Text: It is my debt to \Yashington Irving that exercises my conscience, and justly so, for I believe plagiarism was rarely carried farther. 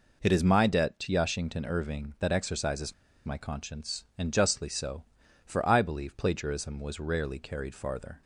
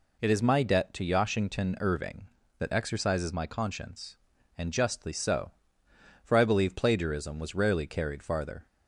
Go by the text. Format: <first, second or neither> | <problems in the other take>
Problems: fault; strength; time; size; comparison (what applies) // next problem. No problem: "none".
second | pauses between "exercises" and "my"; slight; at 2.9 s; 0.31 s long